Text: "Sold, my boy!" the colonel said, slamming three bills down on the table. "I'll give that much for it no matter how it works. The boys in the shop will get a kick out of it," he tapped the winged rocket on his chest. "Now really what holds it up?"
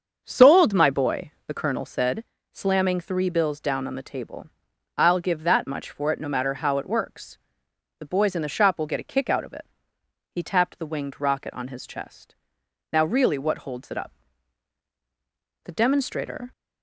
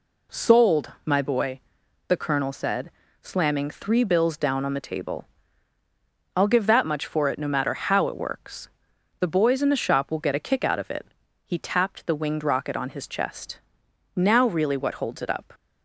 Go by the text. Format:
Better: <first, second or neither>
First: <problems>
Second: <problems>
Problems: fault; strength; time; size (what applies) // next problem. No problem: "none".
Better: second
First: starts louder than the rest; until 1.2 s; 7 dB // goes on to say "The demonstrator"; noticeable; from 15.6 s on; 0.88 s long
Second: none